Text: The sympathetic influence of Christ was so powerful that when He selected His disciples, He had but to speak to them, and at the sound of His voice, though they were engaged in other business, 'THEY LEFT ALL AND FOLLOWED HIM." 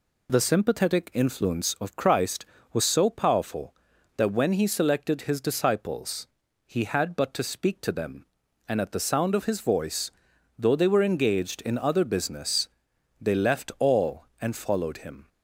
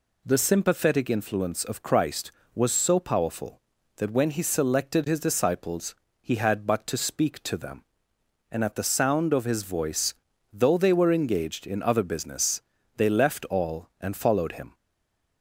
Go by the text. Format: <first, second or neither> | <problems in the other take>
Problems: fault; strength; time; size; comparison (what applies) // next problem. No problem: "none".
first | stays silent after the last word; slight; from 14.7 s on; 0.7 s long